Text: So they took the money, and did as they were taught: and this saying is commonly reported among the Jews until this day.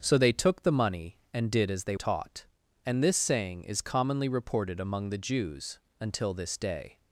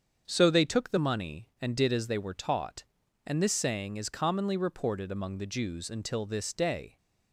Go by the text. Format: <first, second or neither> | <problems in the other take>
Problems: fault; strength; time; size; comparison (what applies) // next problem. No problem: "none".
second | starts louder than the rest; until 1.0 s; 7 dB; strong in the second // skips "were"; at 1.9 s // pauses between "Jews" and "until"; slight; at 5.7 s; 0.22 s long